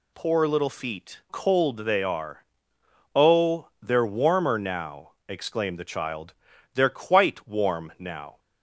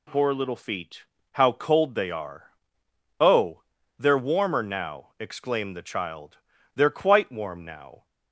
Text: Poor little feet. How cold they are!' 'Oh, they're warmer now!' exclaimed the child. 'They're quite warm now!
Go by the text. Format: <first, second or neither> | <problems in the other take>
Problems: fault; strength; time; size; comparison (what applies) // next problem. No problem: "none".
second | skips "How"; at 1.2 s